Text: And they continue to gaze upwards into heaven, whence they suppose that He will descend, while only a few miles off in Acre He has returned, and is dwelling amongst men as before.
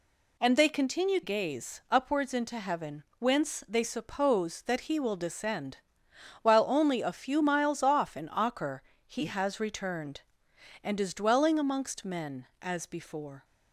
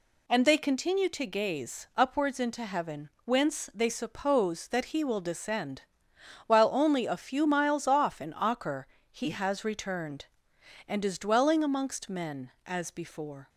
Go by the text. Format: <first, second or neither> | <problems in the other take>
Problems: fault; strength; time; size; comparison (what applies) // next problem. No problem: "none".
second | skips "to"; at 1.2 s // pauses between "Acre" and "He"; slight; at 8.8 s; 0.24 s long; slight in the second